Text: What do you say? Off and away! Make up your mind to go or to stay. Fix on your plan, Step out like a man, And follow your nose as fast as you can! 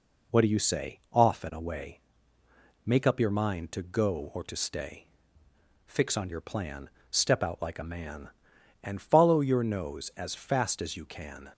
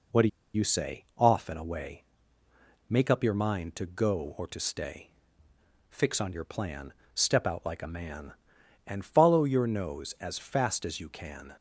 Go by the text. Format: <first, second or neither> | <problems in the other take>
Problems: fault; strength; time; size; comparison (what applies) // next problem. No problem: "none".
first | pauses between "do" and "you"; slight; at 0.2 s; 0.26 s long